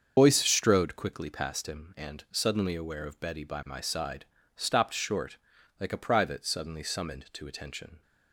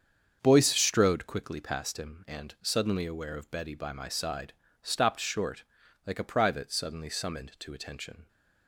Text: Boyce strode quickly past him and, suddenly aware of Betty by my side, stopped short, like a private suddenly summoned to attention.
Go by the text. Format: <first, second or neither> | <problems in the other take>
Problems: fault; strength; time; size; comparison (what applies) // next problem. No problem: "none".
second | loses the start of "Boyce"; at 0.1 s; 65 ms // starts louder than the rest; until 1.1 s; 7 dB; strong in the second